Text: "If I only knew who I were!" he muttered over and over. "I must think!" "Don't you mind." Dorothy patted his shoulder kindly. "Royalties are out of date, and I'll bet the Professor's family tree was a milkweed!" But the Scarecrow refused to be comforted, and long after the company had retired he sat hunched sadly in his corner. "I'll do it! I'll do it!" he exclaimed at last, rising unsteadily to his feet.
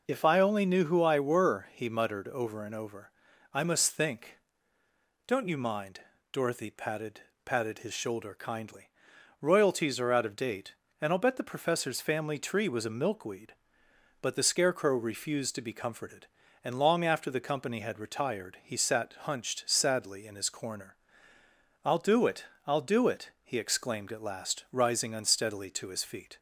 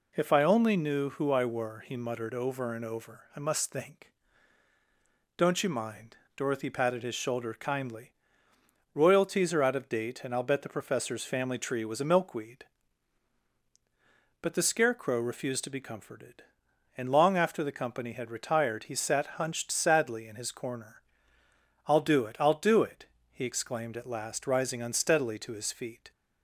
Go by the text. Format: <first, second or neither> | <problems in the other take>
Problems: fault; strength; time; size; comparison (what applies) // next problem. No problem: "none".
second | says "patted" twice; at 7.4 s